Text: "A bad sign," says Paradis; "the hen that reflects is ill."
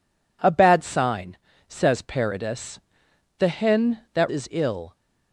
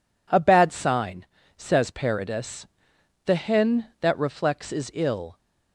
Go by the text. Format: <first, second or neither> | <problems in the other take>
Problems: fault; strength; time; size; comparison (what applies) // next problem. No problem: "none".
second | skips "reflects"; at 4.2 s